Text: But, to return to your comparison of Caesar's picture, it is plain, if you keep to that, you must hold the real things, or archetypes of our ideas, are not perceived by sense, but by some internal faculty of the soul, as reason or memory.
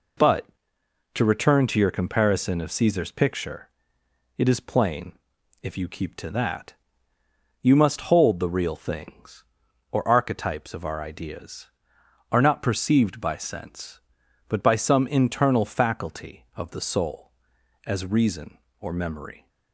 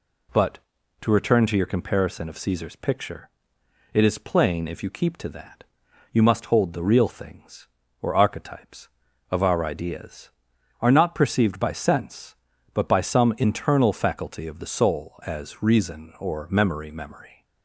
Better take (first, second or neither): first